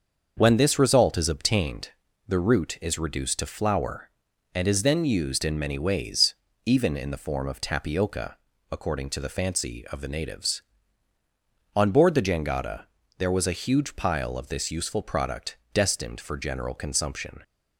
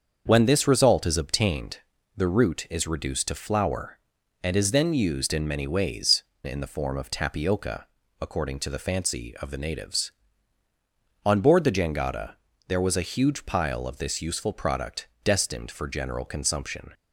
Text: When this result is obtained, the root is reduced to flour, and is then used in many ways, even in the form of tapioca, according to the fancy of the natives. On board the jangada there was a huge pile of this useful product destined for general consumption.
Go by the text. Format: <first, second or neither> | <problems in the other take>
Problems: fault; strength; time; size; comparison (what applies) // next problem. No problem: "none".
first | starts louder than the rest; until 1.2 s; 6.5 dB; also in the first // skips "even"; at 6.3 s // pauses between "jangada" and "there"; slight; at 12.3 s; 0.34 s long; slight in the first // pauses between "product" and "destined"; slight; at 15.0 s; 0.16 s long; slight in the first